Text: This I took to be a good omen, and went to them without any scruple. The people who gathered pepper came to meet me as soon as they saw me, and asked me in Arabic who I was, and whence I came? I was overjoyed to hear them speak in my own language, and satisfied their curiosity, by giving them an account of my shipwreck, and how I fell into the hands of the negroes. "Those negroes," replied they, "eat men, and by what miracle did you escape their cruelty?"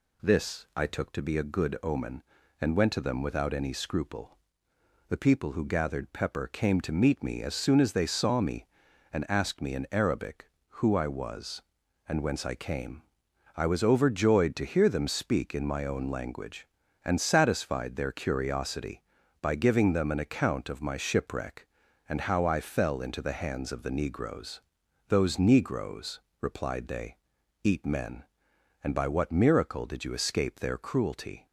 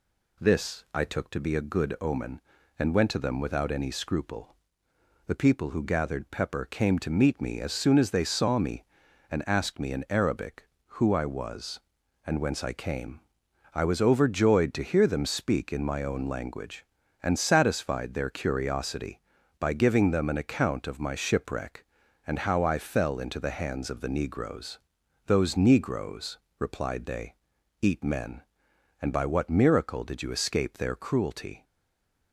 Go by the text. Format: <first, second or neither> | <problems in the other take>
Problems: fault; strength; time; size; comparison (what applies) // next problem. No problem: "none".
first | stays silent after the last word; slight; from 31.6 s on; 0.7 s long